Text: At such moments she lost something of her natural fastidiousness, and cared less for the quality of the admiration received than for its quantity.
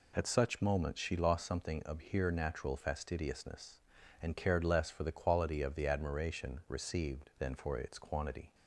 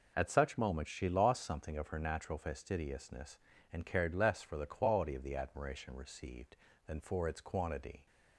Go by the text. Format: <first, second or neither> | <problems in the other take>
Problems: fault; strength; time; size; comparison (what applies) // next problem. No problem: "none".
second | says "here" for "her"; at 1.9 s